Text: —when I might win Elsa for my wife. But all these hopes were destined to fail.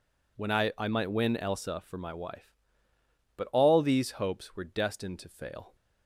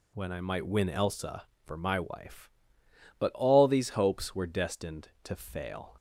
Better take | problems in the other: second | says "I" twice; at 0.7 s

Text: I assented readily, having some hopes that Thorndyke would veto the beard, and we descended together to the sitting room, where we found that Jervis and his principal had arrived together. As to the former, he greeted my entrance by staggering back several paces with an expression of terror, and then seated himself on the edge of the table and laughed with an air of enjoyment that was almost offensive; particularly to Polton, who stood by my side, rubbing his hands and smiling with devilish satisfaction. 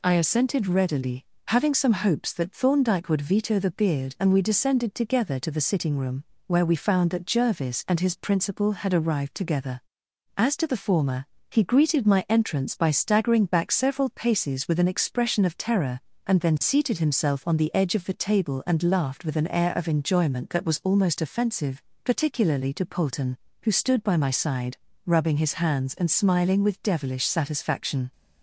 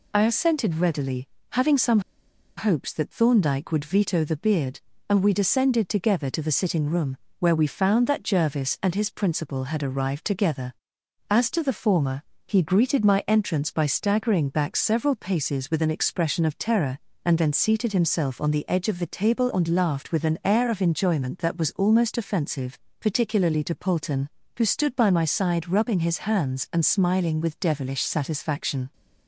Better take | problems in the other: first | pauses between "some" and "hopes"; noticeable; at 1.9 s; 0.57 s long

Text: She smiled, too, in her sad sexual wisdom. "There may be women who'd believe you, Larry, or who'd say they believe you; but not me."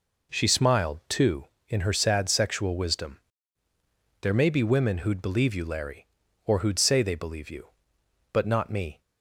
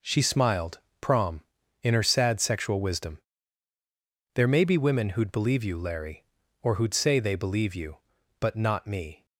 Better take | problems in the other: first | says "prom" for "too"; at 0.9 s

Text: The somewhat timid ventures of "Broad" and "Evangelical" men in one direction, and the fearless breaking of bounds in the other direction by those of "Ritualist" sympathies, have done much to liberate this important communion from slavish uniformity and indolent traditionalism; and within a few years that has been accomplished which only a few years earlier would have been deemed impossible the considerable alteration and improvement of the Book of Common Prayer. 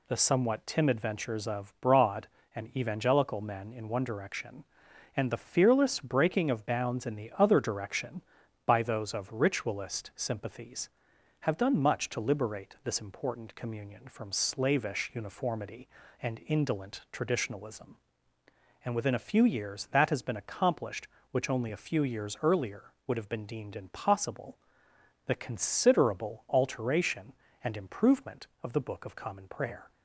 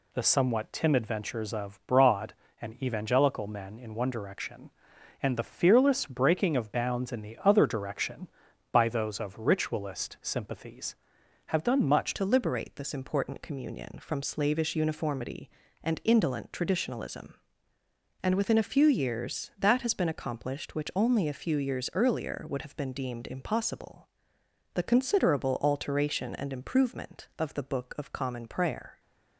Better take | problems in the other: first | changes voice at "to"; from 12.1 s on; 16.8 s long // pauses between "impossible" and "the"; noticeable; at 24.0 s; 0.66 s long; noticeable in the first

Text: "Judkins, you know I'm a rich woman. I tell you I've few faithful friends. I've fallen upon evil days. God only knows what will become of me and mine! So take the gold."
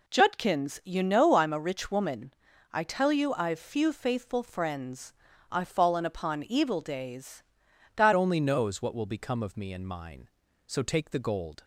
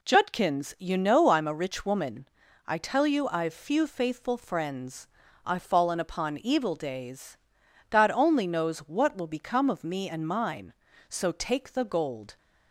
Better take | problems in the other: second | changes voice at "only"; from 8.1 s on; 3.5 s long

